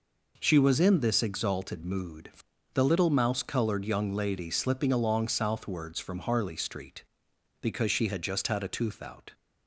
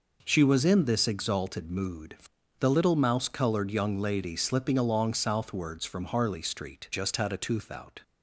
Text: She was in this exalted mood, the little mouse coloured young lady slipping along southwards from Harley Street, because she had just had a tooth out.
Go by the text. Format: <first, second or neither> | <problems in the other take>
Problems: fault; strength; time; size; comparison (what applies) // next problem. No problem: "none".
first | skips "because she had"; at 6.9 s